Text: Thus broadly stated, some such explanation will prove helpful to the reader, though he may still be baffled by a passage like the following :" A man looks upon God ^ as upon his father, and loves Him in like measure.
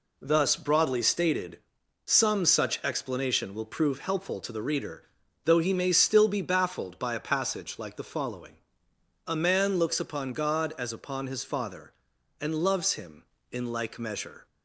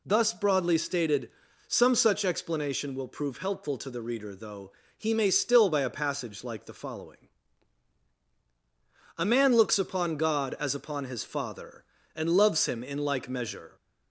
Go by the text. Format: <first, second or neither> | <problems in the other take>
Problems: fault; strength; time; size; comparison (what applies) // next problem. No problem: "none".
first | pauses between "though" and "he"; slight; at 4.7 s; 0.26 s long // skips "be baffled"; at 5.6 s